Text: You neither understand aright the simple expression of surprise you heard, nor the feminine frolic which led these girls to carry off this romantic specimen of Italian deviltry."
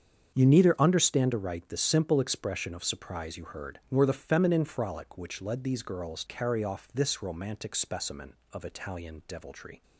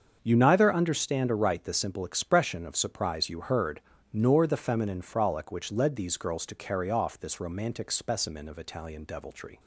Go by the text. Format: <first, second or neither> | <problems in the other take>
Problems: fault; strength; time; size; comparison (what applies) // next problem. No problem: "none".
second | starts louder than the rest; strong; until 1.3 s; 7.5 dB; also in the second // skips "to"; at 6.2 s